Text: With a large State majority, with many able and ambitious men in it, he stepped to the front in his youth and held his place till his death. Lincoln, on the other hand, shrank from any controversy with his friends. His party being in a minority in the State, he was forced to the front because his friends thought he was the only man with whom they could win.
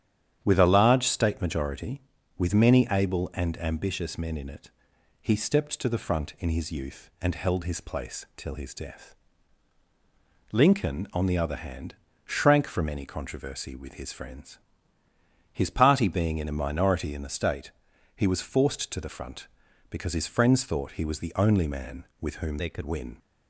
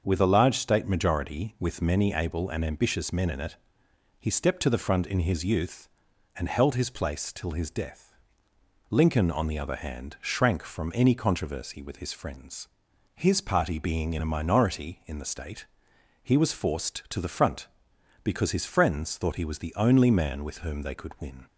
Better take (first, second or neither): second